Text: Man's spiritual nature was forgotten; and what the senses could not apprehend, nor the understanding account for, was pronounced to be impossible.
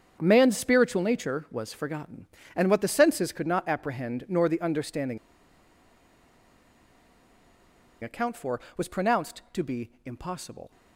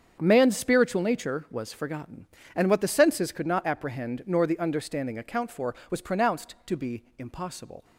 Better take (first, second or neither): second